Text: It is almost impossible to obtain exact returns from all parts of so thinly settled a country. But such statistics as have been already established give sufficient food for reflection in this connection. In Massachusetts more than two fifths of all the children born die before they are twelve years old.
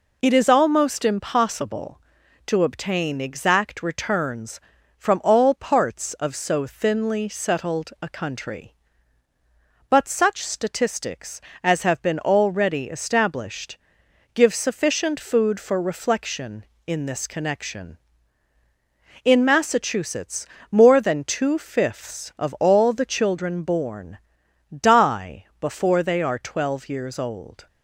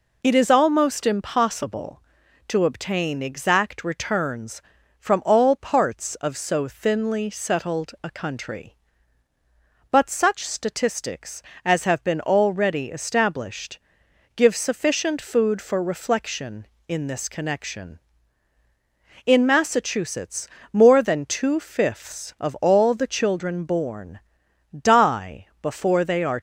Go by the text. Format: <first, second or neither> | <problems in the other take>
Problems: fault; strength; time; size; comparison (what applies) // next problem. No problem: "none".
first | pauses between "established" and "give"; noticeable; at 13.7 s; 0.56 s long; noticeable in the first // pauses between "Massachusetts" and "more"; slight; at 20.4 s; 0.24 s long; slight in the first // pauses between "born" and "die"; noticeable; at 24.1 s; 0.58 s long; noticeable in the first // pauses between "die" and "before"; slight; at 25.4 s; 0.16 s long; slight in the first // stops before "twelve years old"; at 26.3 s